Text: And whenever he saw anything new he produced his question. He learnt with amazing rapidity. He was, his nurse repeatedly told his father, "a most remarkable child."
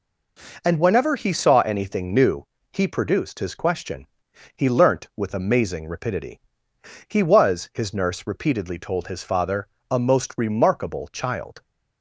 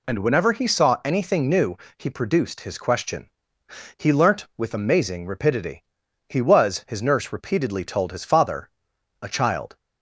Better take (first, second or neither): first